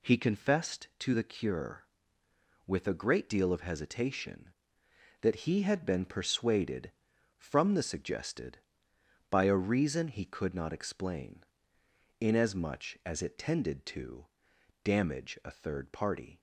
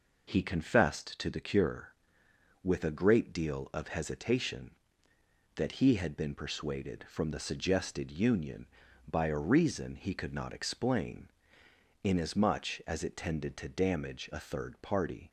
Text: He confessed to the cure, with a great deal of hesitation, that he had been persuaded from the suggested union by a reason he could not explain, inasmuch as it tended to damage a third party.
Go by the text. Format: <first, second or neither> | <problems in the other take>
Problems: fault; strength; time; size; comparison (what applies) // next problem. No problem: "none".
second | skips "union"; at 8.9 s // pauses between "to" and "damage"; noticeable; at 14.2 s; 0.58 s long